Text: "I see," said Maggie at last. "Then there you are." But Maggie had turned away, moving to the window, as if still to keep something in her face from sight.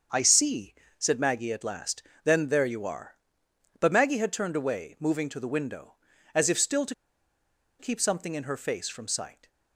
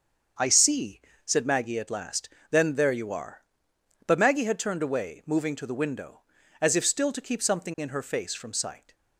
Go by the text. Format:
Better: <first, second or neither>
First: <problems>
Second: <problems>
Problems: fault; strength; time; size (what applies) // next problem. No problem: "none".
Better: second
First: starts louder than the rest; until 1.3 s; 6.5 dB // pauses between "to" and "keep"; noticeable; at 6.9 s; 0.85 s long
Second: starts louder than the rest; until 1.6 s; 7 dB